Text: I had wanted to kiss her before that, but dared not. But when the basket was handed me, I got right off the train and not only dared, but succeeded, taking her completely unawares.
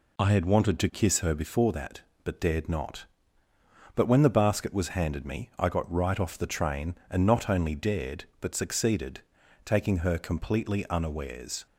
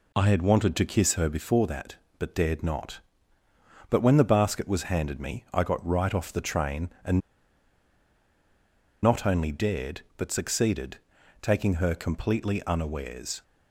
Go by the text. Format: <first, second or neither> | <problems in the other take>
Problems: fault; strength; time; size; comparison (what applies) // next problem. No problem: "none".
first | pauses between "and" and "not"; strong; at 7.1 s; 1.8 s long